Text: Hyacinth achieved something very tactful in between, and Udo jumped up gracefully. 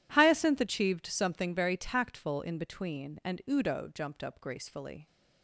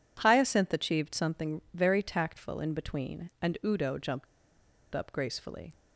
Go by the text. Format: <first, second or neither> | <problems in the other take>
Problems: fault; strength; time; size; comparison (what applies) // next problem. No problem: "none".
first | pauses between "jumped" and "up"; noticeable; at 4.2 s; 0.67 s long